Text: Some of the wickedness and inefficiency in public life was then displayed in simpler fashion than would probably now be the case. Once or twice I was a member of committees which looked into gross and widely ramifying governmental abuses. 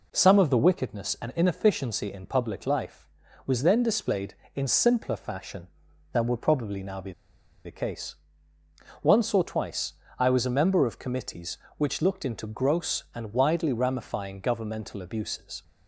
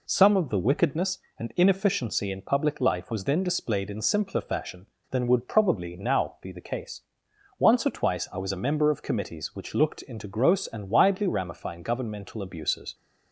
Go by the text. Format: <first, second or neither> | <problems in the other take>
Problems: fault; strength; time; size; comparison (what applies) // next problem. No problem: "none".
second | pauses between "be" and "the"; noticeable; at 7.1 s; 0.53 s long // pauses between "twice" and "I"; slight; at 9.9 s; 0.26 s long